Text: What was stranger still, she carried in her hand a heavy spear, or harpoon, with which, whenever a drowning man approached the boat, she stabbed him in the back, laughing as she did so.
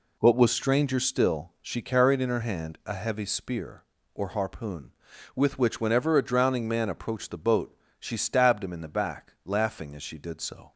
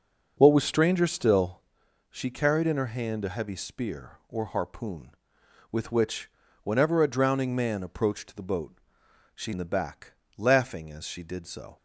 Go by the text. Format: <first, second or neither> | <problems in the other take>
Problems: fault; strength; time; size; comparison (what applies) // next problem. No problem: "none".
first | skips "stabbed him"; at 9.5 s